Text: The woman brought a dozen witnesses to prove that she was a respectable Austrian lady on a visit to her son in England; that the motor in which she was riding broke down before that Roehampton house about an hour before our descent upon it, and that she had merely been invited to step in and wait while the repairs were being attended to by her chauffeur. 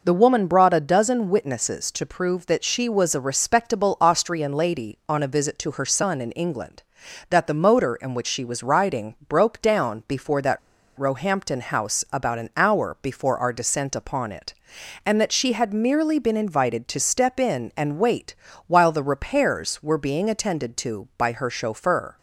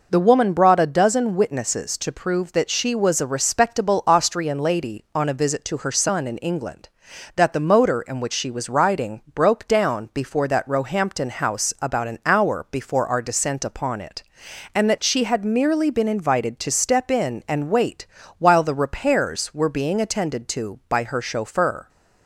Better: second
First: pauses between "riding" and "broke"; slight; at 9.1 s; 0.16 s long // pauses between "that" and "Roehampton"; at 10.5 s; 0.37 s long // pauses between "wait" and "while"; slight; at 18.3 s; 0.32 s long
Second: pauses between "riding" and "broke"; slight; at 9.2 s; 0.16 s long // pauses between "wait" and "while"; slight; at 18.0 s; 0.32 s long

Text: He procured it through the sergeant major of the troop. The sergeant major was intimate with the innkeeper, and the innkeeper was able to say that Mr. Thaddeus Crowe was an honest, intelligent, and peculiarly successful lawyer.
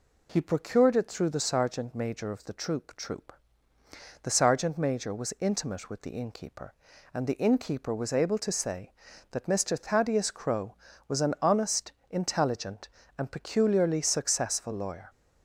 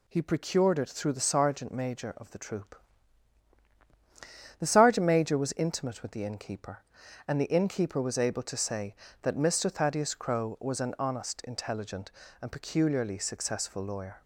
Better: second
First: says "troop" twice; at 2.9 s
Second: none

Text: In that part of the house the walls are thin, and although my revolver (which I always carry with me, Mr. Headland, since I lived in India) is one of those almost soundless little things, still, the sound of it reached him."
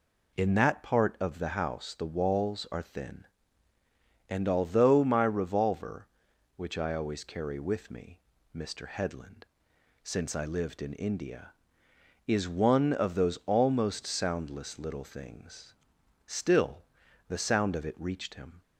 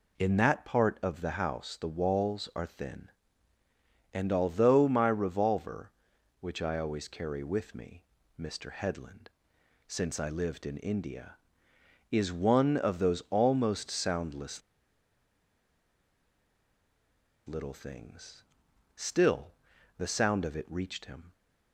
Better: first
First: none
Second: pauses between "soundless" and "little"; strong; at 14.6 s; 2.8 s long

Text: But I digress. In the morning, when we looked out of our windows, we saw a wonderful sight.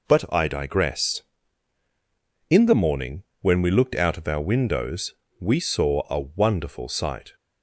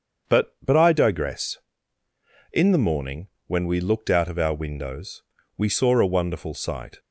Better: first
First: none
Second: starts louder than the rest; until 1.3 s; 7 dB // says "But" twice; at 0.6 s

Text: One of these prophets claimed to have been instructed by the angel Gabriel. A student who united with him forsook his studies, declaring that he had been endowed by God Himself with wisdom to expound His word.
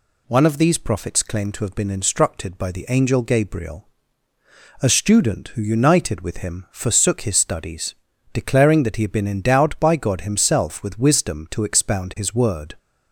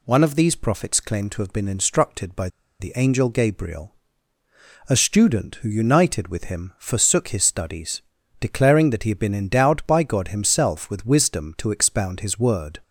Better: first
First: none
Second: pauses between "by" and "the"; slight; at 2.4 s; 0.32 s long

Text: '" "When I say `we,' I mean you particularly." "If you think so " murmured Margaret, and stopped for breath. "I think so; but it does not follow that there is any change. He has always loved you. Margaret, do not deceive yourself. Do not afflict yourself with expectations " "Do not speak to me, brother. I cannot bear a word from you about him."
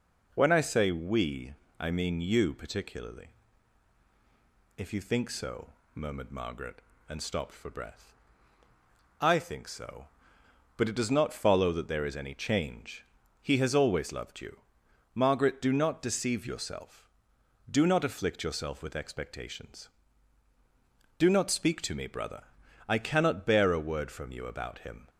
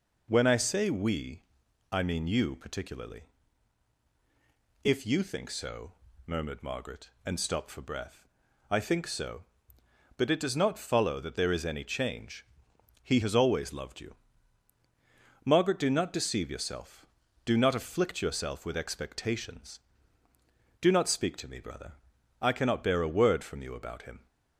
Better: neither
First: none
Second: none

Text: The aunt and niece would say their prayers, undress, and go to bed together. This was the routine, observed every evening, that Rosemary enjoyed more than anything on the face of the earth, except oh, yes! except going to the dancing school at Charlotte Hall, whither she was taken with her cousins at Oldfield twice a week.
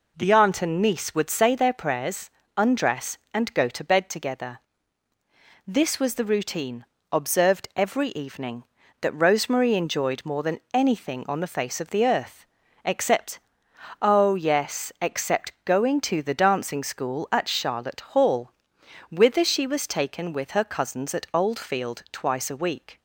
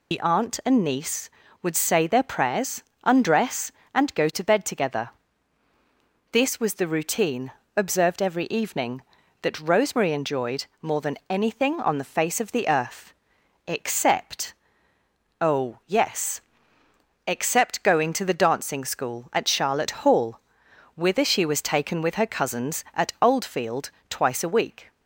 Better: first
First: pauses between "except" and "oh"; noticeable; at 13.3 s; 0.62 s long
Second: loses the start of "The"; at 0.1 s; 65 ms // pauses between "enjoyed" and "more"; slight; at 10.6 s; 0.16 s long // pauses between "except" and "oh"; noticeable; at 14.5 s; 0.88 s long // pauses between "Oldfield" and "twice"; slight; at 23.9 s; 0.20 s long

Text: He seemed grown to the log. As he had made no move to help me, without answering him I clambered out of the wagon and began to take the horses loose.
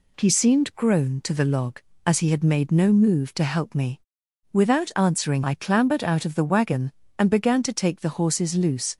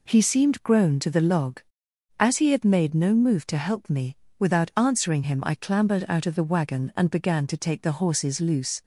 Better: second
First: skips "him"; at 5.4 s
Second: none

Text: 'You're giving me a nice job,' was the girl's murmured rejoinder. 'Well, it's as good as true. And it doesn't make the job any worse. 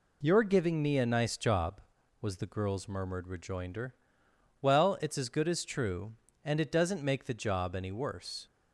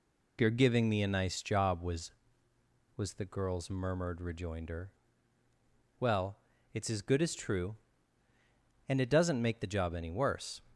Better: first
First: none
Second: says "was" twice; at 2.9 s

